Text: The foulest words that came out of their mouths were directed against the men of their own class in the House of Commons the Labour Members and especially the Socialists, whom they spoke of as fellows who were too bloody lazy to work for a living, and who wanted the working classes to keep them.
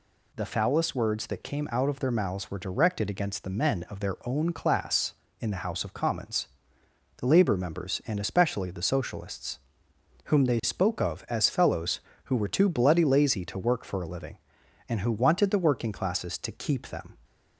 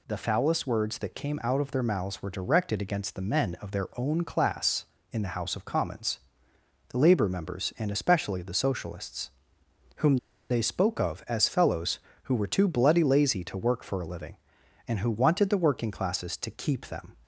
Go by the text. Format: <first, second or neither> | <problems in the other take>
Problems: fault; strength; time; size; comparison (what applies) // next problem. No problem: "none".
first | pauses between "Commons" and "the"; noticeable; at 6.1 s; 0.70 s long; noticeable in the first // pauses between "whom" and "they"; slight; at 10.1 s; 0.32 s long